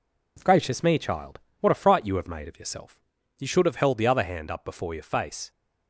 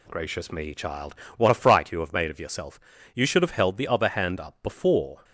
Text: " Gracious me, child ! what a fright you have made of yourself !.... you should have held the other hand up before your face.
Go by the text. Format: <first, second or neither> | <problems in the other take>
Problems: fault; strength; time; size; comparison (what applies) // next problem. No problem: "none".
first | stops before "your face"; at 5.2 s